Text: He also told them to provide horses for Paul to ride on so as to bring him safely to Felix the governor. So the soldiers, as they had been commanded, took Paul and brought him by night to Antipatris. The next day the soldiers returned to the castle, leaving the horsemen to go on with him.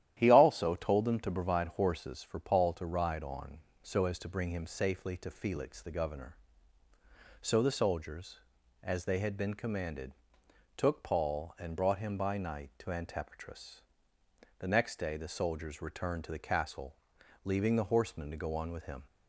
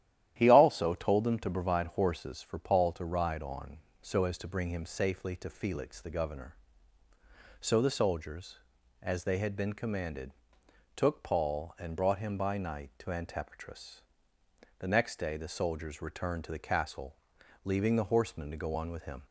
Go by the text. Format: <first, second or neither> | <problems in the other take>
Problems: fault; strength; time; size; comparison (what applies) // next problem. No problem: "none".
neither | starts louder than the rest; strong; the same in both